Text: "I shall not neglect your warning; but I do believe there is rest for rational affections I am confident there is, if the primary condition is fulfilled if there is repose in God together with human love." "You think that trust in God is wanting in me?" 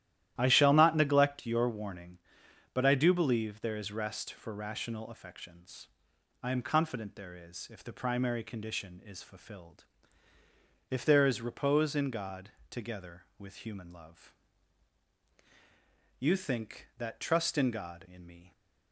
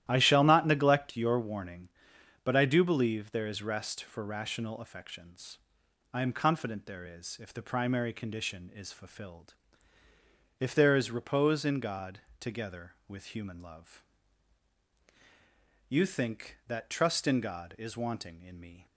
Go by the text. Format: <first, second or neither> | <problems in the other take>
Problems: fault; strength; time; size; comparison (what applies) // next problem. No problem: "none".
second | starts louder than the rest; strong; until 1.3 s; 12.5 dB; strong in the second // pauses between "affections" and "I"; noticeable; at 5.8 s; 0.54 s long; noticeable in the second // pauses between "fulfilled" and "if"; at 9.8 s; 1.0 s long; also in the second // pauses between "God" and "together"; slight; at 12.4 s; 0.18 s long; slight in the second // skips "is wanting"; at 18.0 s